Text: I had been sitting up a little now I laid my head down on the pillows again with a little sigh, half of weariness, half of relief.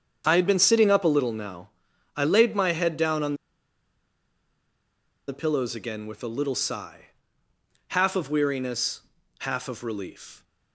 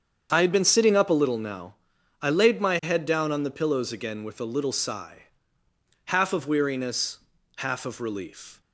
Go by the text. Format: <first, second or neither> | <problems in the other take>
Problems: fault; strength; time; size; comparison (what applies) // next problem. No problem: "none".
second | starts louder than the rest; strong; until 1.3 s; 7.5 dB; strong in the second // pauses between "now" and "I"; noticeable; at 1.6 s; 0.48 s long; noticeable in the second // pauses between "on" and "the"; strong; at 3.3 s; 1.9 s long